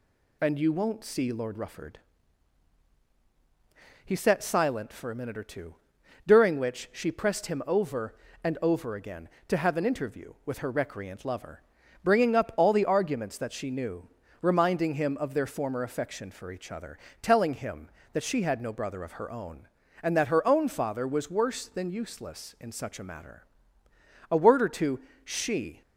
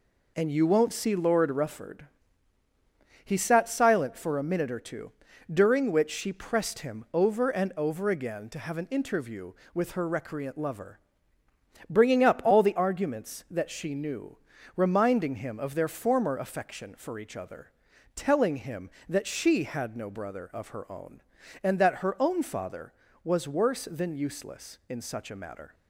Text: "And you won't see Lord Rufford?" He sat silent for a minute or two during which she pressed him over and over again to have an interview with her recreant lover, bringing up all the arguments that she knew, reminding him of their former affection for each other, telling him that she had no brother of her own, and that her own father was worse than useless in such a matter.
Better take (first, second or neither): second